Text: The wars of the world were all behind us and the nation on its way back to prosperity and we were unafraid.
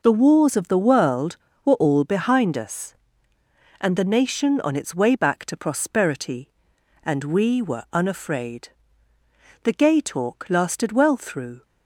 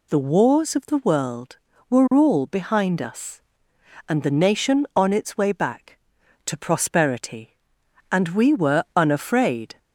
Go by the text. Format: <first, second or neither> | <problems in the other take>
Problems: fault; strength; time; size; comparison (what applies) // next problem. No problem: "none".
second | goes on to say "The gay talk lasted well through"; strong; from 9.6 s on; 2.0 s long